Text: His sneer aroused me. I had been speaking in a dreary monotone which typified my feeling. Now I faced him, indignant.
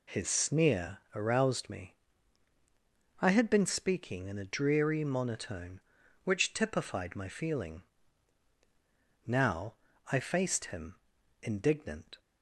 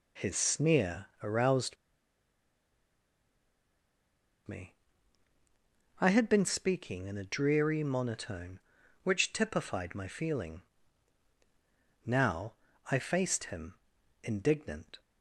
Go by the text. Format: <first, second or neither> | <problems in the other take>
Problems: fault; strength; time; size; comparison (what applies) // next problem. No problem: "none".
first | pauses between "sneer" and "aroused"; slight; at 1.0 s; 0.18 s long; slight in the first // pauses between "aroused" and "me"; strong; at 1.7 s; 2.7 s long // pauses between "Now" and "I"; slight; at 12.5 s; 0.36 s long; slight in the first